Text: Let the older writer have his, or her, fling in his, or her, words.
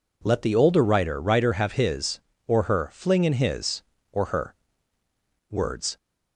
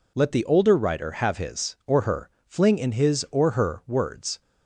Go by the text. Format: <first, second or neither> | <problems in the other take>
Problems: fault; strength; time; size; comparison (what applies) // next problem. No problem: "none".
second | says "writer" twice; at 1.2 s